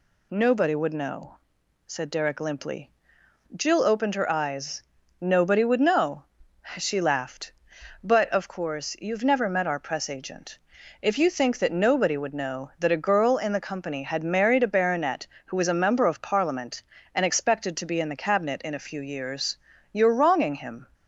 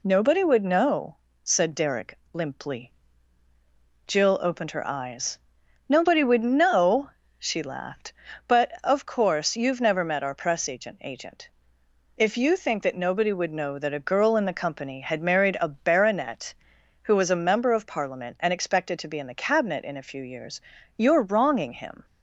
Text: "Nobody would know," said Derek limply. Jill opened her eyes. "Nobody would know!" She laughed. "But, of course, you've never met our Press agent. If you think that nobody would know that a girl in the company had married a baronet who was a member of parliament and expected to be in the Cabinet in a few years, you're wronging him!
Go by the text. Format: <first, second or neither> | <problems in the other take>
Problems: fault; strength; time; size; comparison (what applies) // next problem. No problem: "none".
first | pauses between "Derek" and "limply"; slight; at 2.1 s; 0.16 s long // says "agent" twice; at 11.0 s